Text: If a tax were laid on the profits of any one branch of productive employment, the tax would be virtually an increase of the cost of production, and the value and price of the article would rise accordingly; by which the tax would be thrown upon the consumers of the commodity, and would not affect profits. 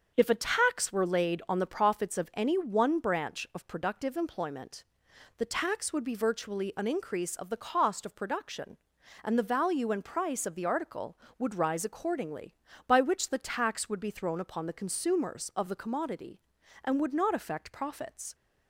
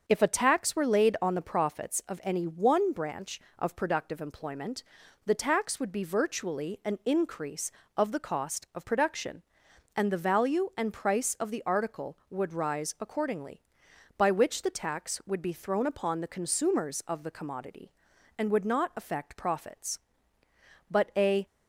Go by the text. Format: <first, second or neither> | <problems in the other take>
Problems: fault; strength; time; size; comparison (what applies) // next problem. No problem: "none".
first | starts louder than the rest; until 1.0 s; 6.5 dB; also in the first // goes on to say "But a"; from 20.8 s on; 0.56 s long